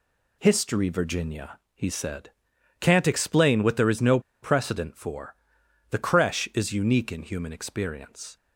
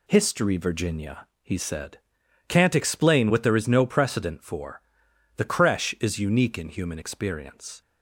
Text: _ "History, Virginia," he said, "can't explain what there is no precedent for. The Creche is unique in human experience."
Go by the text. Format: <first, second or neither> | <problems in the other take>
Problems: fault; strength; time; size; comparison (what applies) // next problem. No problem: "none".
second | pauses between "no" and "precedent"; slight; at 4.1 s; 0.24 s long